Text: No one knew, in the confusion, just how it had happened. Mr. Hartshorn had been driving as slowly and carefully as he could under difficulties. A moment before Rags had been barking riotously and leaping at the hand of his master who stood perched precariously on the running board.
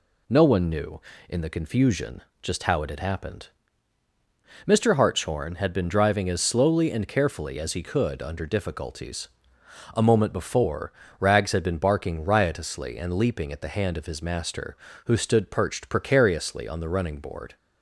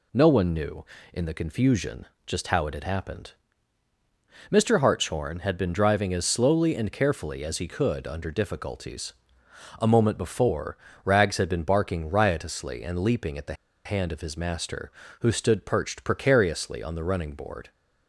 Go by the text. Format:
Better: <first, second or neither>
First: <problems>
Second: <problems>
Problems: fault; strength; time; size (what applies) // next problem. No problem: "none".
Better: first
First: pauses between "before" and "Rags"; slight; at 10.9 s; 0.26 s long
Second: pauses between "before" and "Rags"; slight; at 10.7 s; 0.26 s long // pauses between "the" and "hand"; slight; at 13.5 s; 0.31 s long